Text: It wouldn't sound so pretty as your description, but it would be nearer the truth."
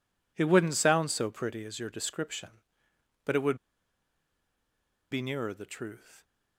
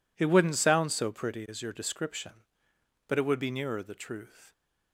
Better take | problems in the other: second | pauses between "would" and "be"; strong; at 3.5 s; 1.5 s long

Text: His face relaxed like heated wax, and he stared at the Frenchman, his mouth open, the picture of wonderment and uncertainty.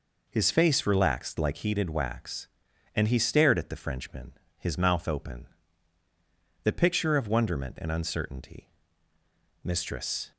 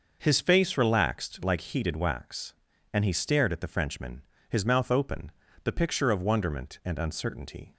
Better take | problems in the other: second | goes on to say "Mistress"; noticeable; from 9.6 s on; 0.68 s long

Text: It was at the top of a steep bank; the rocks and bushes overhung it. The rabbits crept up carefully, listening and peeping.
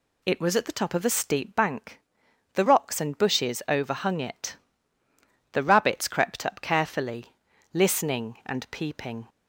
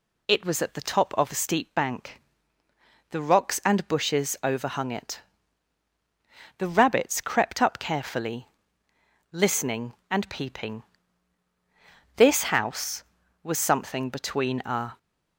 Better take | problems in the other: first | goes on to say "This house was something between a"; strong; from 12.1 s on; 2.8 s long

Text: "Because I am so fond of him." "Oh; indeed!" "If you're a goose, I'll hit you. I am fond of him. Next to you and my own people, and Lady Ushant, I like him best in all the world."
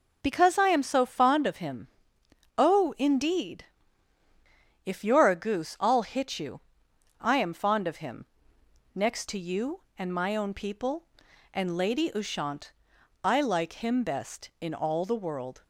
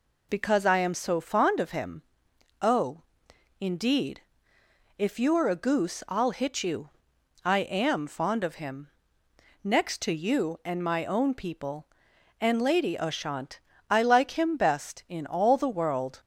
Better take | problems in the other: neither | none

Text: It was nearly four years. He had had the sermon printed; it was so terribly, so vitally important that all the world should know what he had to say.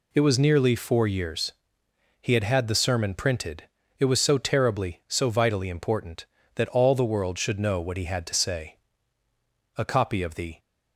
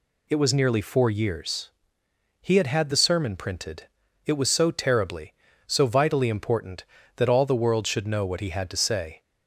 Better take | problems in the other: second | goes on to say "A copy of the"; noticeable; from 9.7 s on; 0.82 s long

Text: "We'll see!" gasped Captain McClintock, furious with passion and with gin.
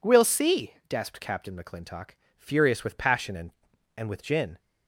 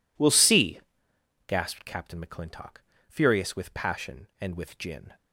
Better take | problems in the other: second | says "and" twice; at 3.9 s

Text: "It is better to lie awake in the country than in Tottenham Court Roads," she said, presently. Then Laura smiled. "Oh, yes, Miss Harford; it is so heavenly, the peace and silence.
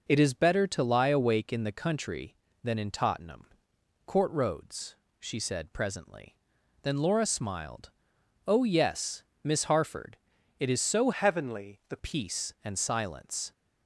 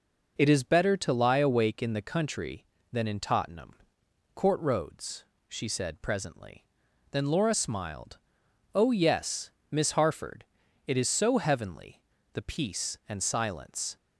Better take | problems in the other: second | pauses between "Tottenham" and "Court"; noticeable; at 3.4 s; 0.60 s long; noticeable in the second // changes voice from "heavenly" to "the"; from 11.1 to 11.9 s; 0.8 s long

